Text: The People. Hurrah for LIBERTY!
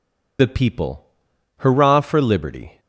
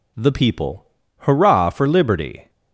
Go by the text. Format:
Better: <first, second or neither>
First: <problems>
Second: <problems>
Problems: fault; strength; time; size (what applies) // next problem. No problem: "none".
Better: second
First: loses the start of "The"; at 0.3 s; 70 ms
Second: none